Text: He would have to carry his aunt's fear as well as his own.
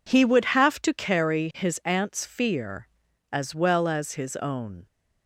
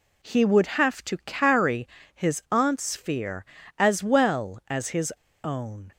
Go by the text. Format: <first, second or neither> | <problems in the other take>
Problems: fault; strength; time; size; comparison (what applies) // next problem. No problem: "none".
first | pauses between "carry" and "his"; slight; at 1.8 s; 0.26 s long // pauses between "his" and "own"; slight; at 5.1 s; 0.31 s long